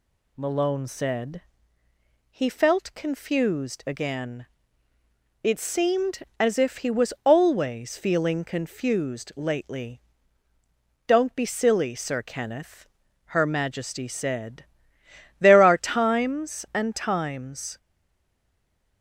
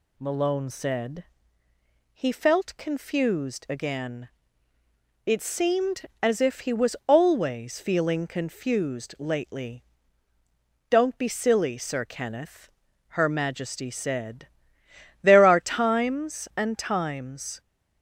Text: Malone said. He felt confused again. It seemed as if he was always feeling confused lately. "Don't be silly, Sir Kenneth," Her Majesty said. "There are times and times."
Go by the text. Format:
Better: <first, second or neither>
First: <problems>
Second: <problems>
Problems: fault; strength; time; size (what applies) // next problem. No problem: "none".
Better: second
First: stays silent after the last word; noticeable; from 17.7 s on; 1.3 s long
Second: none